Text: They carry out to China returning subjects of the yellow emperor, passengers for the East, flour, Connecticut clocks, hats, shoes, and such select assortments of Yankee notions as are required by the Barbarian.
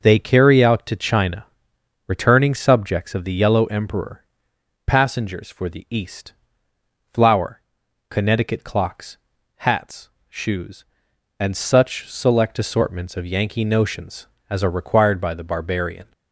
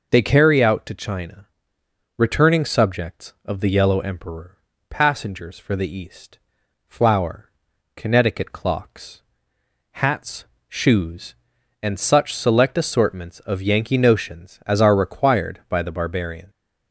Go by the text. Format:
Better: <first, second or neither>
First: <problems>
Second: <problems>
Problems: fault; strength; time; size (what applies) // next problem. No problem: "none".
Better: neither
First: pauses between "China" and "returning"; noticeable; at 1.4 s; 0.62 s long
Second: pauses between "China" and "returning"; noticeable; at 1.4 s; 0.72 s long